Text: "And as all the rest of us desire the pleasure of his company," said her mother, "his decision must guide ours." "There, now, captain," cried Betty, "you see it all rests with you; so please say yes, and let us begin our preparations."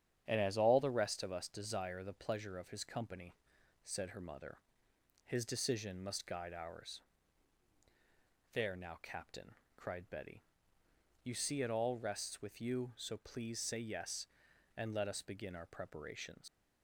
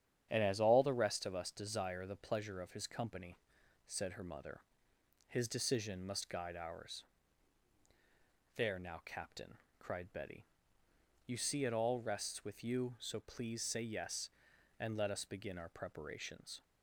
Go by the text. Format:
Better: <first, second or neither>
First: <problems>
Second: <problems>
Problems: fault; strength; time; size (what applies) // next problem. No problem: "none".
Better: second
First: starts louder than the rest; strong; until 1.2 s; 9.5 dB // leaves "preparations" unfinished; at 16.4 s; 115 ms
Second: starts louder than the rest; strong; until 1.3 s; 9.5 dB